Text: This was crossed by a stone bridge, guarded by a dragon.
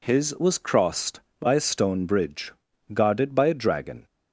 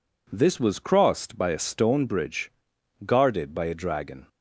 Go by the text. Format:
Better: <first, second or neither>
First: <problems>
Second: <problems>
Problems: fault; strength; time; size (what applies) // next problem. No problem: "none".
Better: second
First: says "His" for "This"; at 0.0 s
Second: none